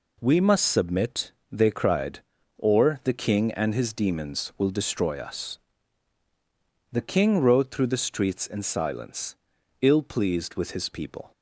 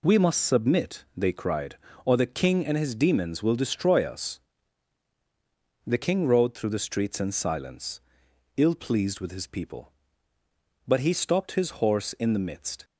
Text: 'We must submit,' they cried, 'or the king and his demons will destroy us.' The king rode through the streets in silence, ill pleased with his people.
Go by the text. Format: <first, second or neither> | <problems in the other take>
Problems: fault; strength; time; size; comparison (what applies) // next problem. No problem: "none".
first | goes on to say "But he stopped his horse in the midst"; strong; from 10.8 s on; 1.9 s long